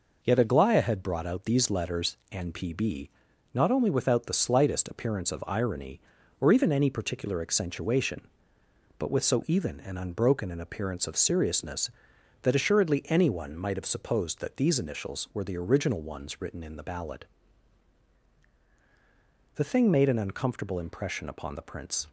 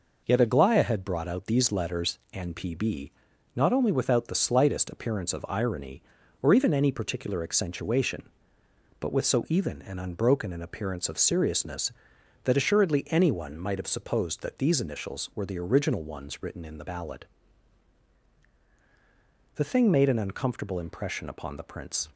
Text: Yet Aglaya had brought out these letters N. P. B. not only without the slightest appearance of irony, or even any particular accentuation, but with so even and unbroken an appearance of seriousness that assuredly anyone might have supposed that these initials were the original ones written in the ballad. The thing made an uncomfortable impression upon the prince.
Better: neither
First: pauses between "B" and "not"; at 3.0 s; 0.44 s long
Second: pauses between "B" and "not"; at 3.1 s; 0.44 s long

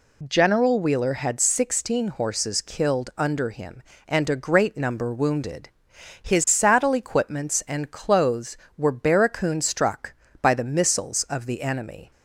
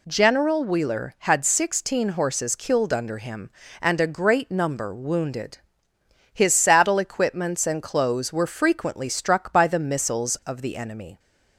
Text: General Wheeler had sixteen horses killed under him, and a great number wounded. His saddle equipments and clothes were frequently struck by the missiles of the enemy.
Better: second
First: says "barracoon" for "frequently"; at 8.9 s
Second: none

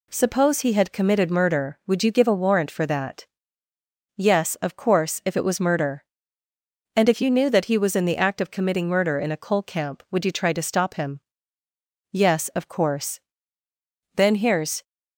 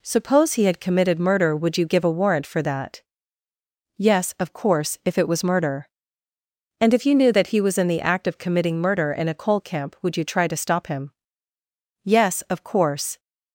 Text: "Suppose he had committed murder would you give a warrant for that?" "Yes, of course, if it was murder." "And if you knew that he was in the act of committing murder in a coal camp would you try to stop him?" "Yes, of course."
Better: second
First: goes on to say "Then here's"; noticeable; from 14.1 s on; 0.68 s long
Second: none

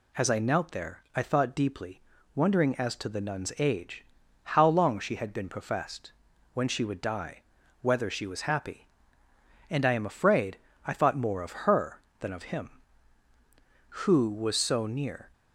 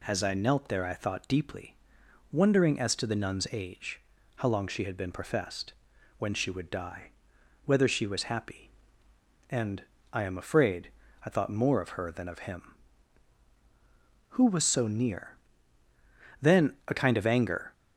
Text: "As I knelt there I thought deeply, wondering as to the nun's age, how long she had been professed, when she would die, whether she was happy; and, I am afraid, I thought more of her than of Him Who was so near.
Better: first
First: none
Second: goes on to say "Then a kind of anger"; from 16.4 s on; 1.3 s long

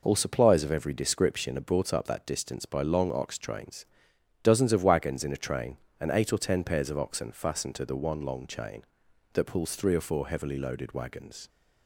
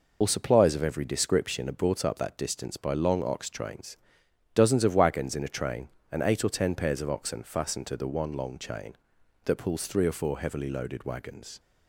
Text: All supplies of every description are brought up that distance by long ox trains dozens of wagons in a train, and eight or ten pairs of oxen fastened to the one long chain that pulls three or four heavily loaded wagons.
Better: first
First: pauses between "trains" and "dozens"; noticeable; at 3.8 s; 0.56 s long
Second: loses the start of "All"; at 0.2 s; 65 ms // pauses between "trains" and "dozens"; noticeable; at 3.9 s; 0.56 s long

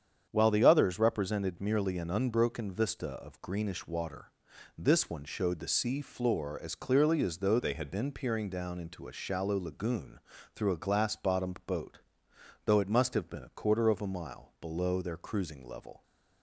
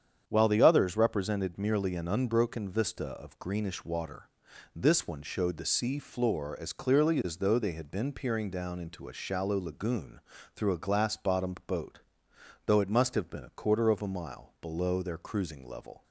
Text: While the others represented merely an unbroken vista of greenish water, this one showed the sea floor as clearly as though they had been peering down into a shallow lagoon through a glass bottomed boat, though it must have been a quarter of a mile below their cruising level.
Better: second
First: starts louder than the rest; strong; until 1.3 s; 8 dB // changes voice from "they" to "had"; from 7.5 to 7.8 s; 0.3 s long // pauses between "lagoon" and "through"; slight; at 10.1 s; 0.34 s long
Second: starts louder than the rest; strong; until 1.2 s; 8 dB // pauses between "lagoon" and "through"; slight; at 10.1 s; 0.34 s long

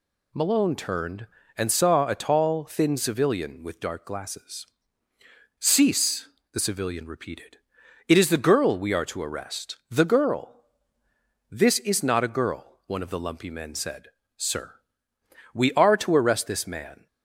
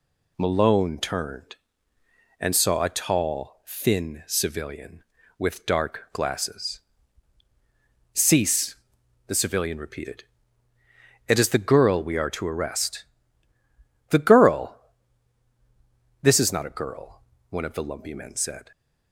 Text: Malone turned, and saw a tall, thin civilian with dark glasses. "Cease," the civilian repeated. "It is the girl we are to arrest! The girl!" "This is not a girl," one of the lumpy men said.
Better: second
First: goes on to say "Sir We are to arrest this man"; strong; from 14.3 s on; 2.7 s long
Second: none

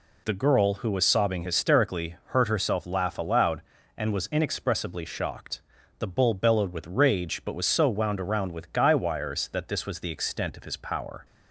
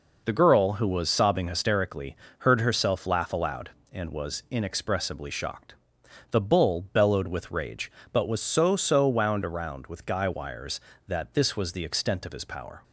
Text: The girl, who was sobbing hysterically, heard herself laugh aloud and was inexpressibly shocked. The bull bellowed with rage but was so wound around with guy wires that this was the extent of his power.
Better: first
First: none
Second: says "so" twice; at 8.7 s

